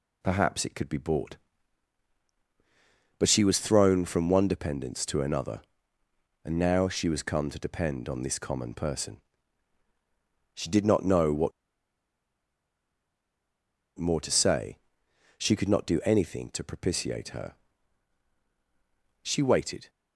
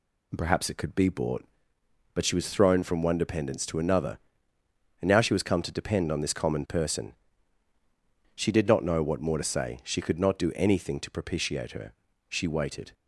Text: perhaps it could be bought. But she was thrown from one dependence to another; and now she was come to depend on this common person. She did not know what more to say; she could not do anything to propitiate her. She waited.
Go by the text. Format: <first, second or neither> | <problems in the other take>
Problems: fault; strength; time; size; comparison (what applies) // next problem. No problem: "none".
second | pauses between "what" and "more"; strong; at 11.5 s; 2.4 s long